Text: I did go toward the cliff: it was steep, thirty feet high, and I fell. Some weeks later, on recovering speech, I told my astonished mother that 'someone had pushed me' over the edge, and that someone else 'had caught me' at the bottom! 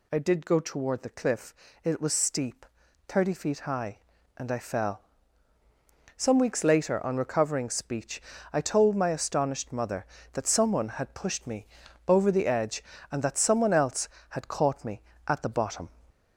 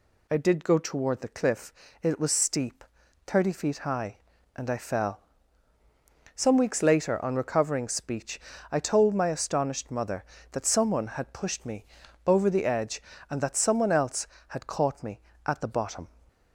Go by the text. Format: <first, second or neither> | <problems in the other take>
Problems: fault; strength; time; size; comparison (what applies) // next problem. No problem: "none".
second | gets louder; slight; throughout; 2.5 dB // pauses between "me" and "over"; at 11.6 s; 0.40 s long; also in the second